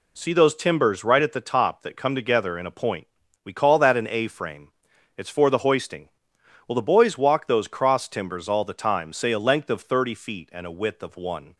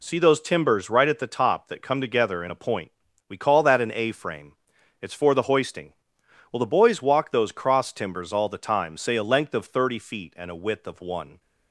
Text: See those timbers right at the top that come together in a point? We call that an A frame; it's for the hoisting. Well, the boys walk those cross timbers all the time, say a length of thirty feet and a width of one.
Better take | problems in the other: neither | none

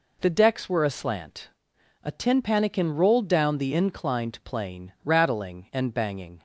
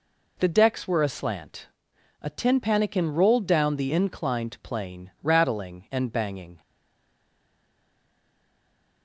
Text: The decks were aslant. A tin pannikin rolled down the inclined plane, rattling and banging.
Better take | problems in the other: first | stays silent after the last word; from 6.6 s on; 2.4 s long

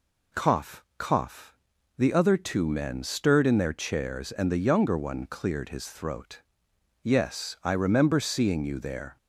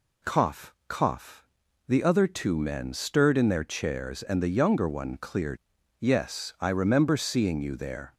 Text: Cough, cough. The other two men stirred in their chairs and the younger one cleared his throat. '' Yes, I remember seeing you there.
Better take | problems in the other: first | skips "his throat"; at 5.6 s

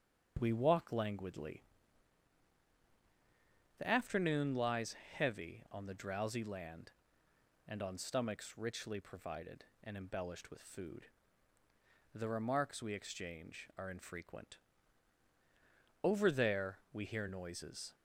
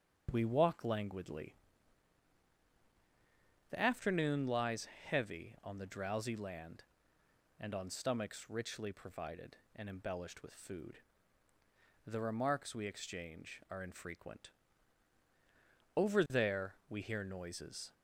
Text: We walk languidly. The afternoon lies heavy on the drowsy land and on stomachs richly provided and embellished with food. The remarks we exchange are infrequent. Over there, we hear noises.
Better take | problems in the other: neither | starts louder than the rest; the same in both // pauses between "lies" and "heavy"; slight; the same in both

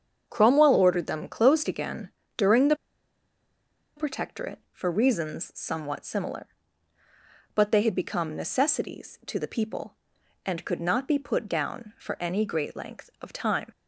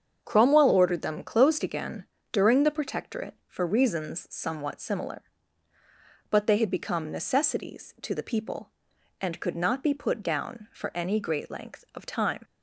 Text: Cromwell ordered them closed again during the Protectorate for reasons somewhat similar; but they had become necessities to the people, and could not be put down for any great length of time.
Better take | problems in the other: second | starts louder than the rest; strong; until 1.2 s; 7.5 dB; strong in the second // pauses between "again" and "during"; slight; at 2.1 s; 0.26 s long; slight in the second // pauses between "the" and "Protectorate"; at 2.7 s; 1.2 s long

